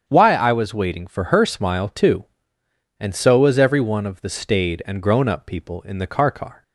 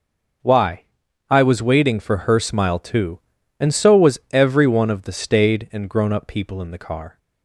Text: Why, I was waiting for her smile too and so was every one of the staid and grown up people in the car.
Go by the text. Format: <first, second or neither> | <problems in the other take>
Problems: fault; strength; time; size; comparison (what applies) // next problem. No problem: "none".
second | starts louder than the rest; strong; until 1.0 s; 8 dB // says "car" twice; at 6.3 s